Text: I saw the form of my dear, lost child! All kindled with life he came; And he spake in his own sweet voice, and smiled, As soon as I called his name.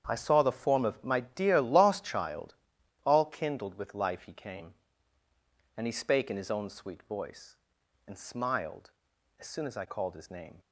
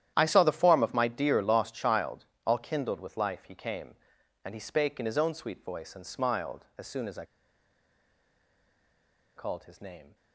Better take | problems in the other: first | starts louder than the rest; strong; until 1.1 s; 11 dB; strong in the first // pauses between "I" and "called"; strong; at 7.2 s; 2.1 s long

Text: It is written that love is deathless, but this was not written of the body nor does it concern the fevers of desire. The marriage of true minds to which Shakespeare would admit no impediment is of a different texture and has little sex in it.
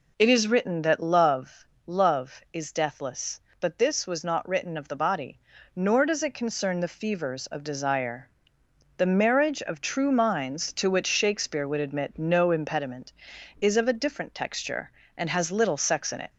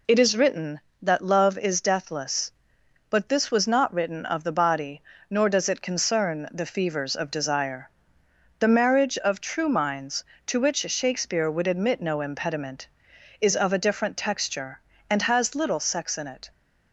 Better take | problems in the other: second | says "love" twice; at 1.8 s // pauses between "body" and "nor"; slight; at 5.3 s; 0.34 s long; slight in the second

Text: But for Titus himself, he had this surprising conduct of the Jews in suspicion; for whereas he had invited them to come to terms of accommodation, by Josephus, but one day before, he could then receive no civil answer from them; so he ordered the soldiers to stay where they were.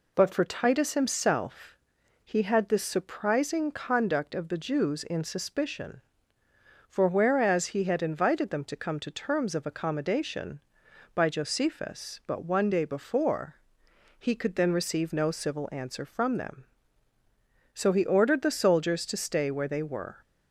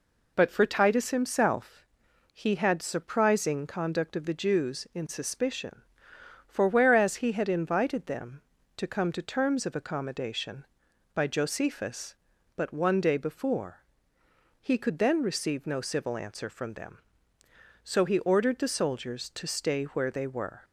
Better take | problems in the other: first | skips "this"; at 2.8 s

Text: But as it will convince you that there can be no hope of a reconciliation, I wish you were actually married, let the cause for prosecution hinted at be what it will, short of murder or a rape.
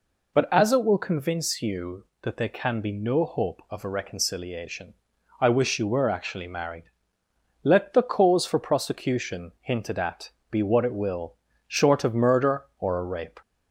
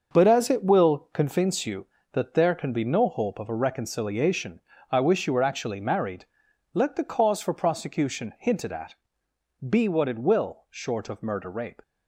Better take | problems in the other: first | starts louder than the rest; noticeable; until 1.1 s; 6 dB // pauses between "at" and "be"; noticeable; at 8.9 s; 0.74 s long; slight in the first // skips "or a"; at 11.4 s

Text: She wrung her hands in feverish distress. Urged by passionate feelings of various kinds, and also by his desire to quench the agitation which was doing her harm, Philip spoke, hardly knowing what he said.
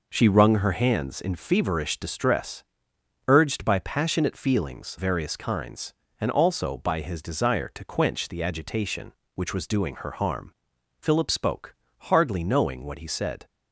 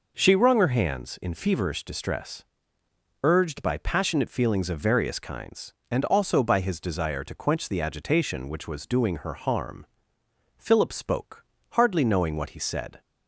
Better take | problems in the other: second | skips "of"; at 4.9 s

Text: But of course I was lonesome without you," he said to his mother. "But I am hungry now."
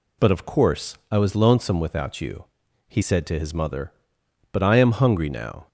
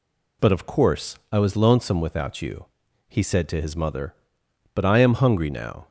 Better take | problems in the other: neither | none

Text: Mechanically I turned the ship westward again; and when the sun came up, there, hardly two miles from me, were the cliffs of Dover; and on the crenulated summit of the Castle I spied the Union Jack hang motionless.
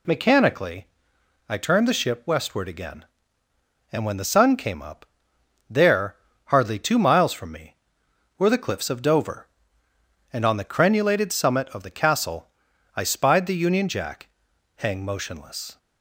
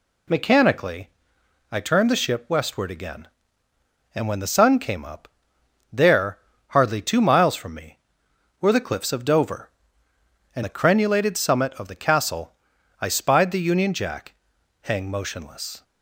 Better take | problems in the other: first | pauses between "Mechanically" and "I"; noticeable; at 1.0 s; 0.62 s long; noticeable in the first // skips "on"; at 10.6 s // pauses between "Castle" and "I"; noticeable; at 12.5 s; 0.46 s long; noticeable in the first // pauses between "Jack" and "hang"; noticeable; at 14.3 s; 0.48 s long; noticeable in the first

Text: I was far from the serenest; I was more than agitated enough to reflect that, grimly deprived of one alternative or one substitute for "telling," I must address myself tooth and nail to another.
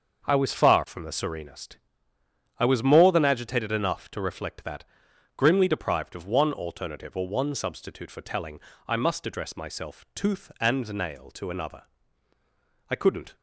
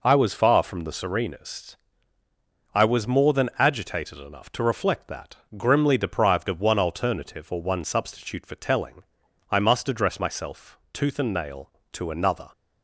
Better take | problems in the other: second | starts louder than the rest; until 1.2 s; 6 dB // goes on to say "I couldn't"; slight; from 12.8 s on; 0.46 s long

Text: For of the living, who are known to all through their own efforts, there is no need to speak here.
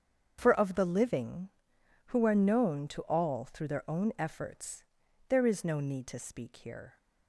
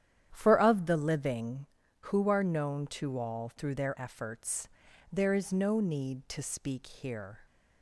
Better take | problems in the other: first | starts louder than the rest; strong; until 1.3 s; 10.5 dB; strong in the first // skips "own"; at 3.9 s

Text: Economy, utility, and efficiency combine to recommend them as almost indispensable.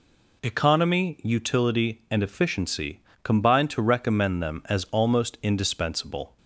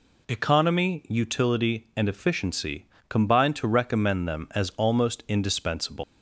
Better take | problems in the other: first | pauses between "efficiency" and "combine"; slight; at 2.8 s; 0.24 s long; slight in the first // leaves "indispensable" unfinished; at 6.0 s; 190 ms

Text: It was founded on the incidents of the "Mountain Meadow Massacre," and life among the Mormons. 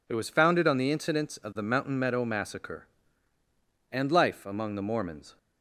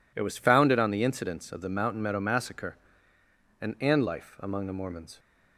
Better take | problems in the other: first | says "and" twice; at 3.7 s

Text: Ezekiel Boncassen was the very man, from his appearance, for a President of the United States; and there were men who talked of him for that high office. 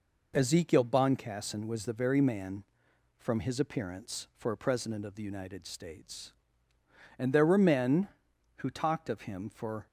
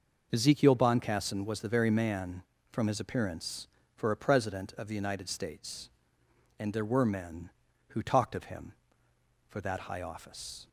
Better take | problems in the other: second | stops before "that high office"; at 9.8 s

